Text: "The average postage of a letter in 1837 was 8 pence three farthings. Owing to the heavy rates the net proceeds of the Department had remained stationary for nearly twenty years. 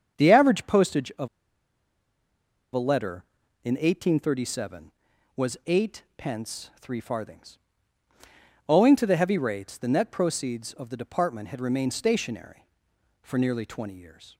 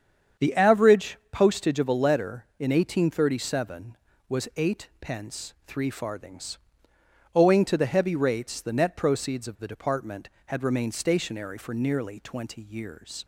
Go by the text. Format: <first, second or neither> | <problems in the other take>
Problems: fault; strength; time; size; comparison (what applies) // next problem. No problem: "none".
second | starts louder than the rest; strong; until 1.2 s; 7.5 dB; strong in the second // pauses between "of" and "a"; strong; at 1.2 s; 1.4 s long